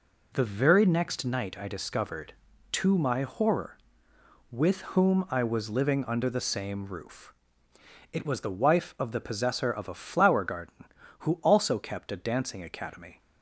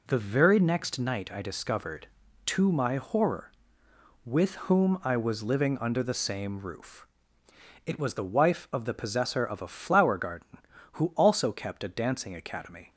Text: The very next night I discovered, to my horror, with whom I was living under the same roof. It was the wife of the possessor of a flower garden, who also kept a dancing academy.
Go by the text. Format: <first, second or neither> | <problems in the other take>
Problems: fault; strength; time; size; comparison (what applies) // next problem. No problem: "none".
neither | pauses between "with" and "whom"; slight; the same in both